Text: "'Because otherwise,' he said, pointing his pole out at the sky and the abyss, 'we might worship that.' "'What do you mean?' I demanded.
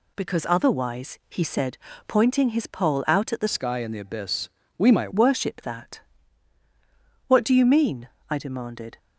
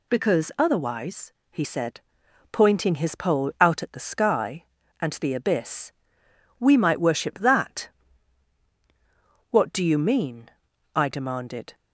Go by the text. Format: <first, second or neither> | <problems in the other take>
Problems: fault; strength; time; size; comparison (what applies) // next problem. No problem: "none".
second | changes voice from "sky" to "might"; from 3.4 to 5.1 s; 1.7 s long